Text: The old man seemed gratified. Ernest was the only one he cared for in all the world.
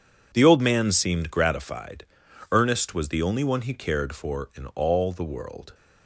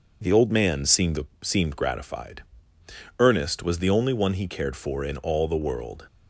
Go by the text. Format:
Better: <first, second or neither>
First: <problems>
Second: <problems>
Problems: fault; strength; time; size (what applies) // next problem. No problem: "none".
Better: first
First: none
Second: says "seemed" twice; at 1.4 s